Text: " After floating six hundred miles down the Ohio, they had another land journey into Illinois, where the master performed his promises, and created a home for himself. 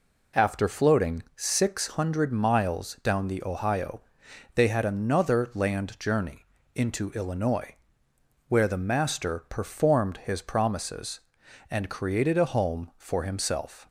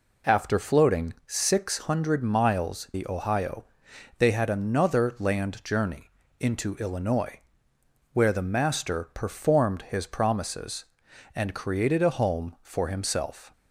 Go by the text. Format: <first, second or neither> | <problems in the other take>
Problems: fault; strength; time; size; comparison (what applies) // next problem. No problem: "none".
first | skips "down"; at 2.9 s // pauses between "journey" and "into"; slight; at 6.0 s; 0.30 s long; slight in the first